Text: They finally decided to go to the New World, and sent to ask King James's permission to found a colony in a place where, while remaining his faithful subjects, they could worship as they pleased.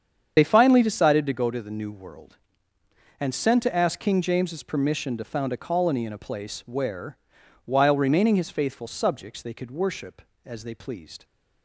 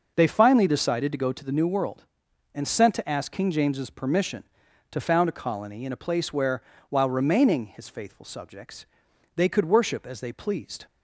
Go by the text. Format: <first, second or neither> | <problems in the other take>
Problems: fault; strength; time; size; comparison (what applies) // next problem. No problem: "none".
second | loses the start of "They"; at 0.3 s; 50 ms // starts louder than the rest; strong; until 1.3 s; 8 dB